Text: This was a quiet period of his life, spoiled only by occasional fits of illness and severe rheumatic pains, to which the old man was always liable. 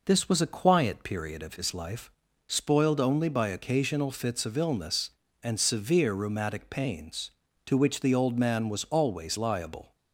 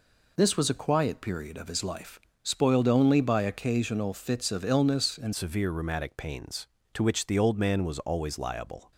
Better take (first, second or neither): first